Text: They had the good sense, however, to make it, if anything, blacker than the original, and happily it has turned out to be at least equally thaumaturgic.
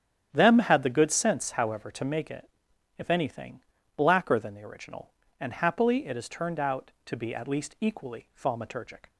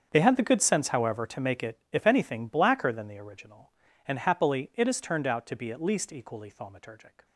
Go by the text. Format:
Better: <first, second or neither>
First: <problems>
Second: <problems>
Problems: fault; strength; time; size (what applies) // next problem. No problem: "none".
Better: second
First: starts louder than the rest; strong; until 1.3 s; 9.5 dB // says "Them" for "They"; at 0.3 s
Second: starts louder than the rest; strong; until 1.1 s; 7.5 dB